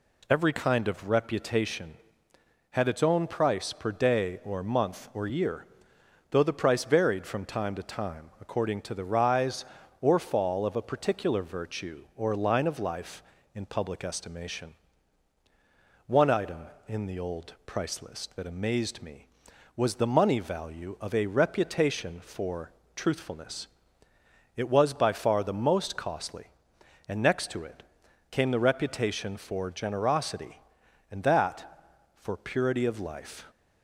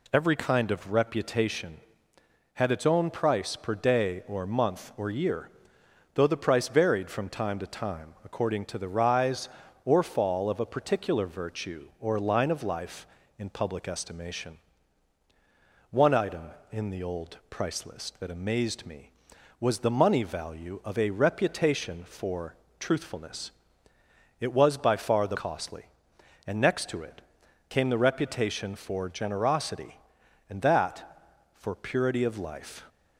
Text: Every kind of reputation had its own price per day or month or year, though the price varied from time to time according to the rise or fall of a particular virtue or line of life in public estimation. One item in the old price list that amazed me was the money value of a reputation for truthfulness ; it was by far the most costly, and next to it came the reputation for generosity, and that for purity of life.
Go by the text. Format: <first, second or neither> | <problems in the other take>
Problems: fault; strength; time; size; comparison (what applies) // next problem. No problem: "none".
first | pauses between "for" and "truthfulness"; slight; at 22.5 s; 0.24 s long; slight in the first // skips "most"; at 25.3 s // pauses between "it" and "came"; noticeable; at 27.2 s; 0.46 s long; noticeable in the first